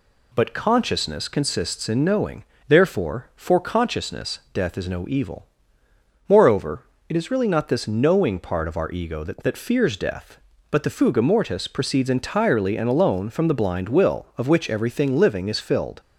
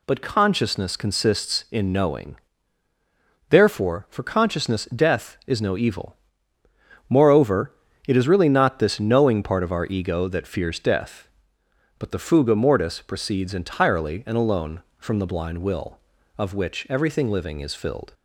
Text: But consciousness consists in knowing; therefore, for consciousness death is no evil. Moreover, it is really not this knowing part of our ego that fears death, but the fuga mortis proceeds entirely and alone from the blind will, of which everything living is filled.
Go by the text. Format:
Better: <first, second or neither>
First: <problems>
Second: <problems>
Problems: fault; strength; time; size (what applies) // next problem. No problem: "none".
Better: second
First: says "that" twice; at 9.4 s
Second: none